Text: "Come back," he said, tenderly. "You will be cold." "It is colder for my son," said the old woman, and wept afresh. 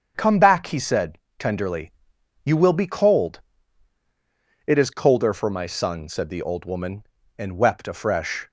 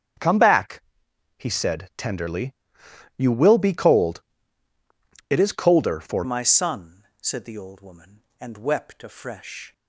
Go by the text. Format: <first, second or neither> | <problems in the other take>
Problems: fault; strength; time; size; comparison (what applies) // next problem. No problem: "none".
first | starts louder than the rest; strong; until 1.7 s; 8 dB; strong in the first // changes voice at "my"; from 6.2 s on; 3.5 s long